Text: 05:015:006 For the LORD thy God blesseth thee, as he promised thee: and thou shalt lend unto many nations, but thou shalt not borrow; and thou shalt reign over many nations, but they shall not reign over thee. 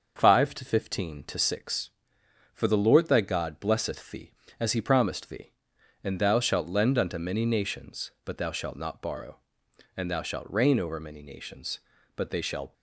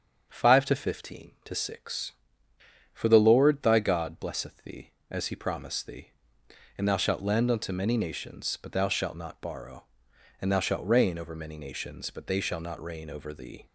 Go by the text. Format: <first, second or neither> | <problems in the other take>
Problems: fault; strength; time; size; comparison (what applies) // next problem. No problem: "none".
second | starts louder than the rest; until 1.1 s; 6 dB; strong in the second // stops before "not reign over thee"; at 12.7 s